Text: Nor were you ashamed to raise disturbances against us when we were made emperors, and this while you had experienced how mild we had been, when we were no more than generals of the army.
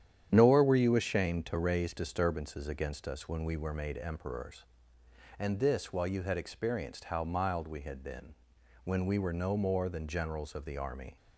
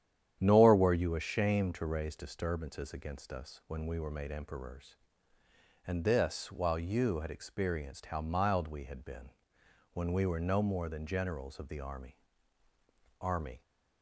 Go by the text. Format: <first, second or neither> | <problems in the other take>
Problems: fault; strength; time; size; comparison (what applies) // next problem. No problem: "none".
first | starts louder than the rest; strong; until 1.4 s; 10 dB; strong in the first // says "army" twice; at 13.1 s